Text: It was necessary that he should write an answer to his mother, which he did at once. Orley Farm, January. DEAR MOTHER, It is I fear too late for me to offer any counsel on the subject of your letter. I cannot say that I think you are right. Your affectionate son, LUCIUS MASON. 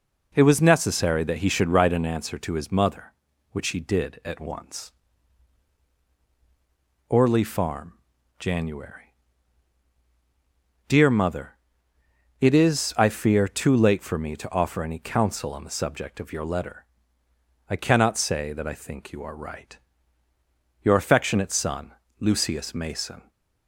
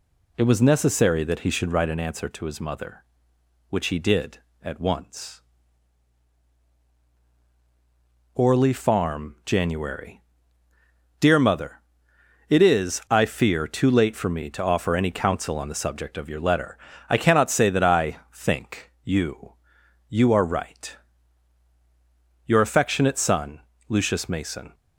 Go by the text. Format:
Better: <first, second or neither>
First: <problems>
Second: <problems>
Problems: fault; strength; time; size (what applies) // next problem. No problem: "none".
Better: first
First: none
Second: pauses between "I" and "think"; slight; at 18.1 s; 0.16 s long // says "you" twice; at 20.0 s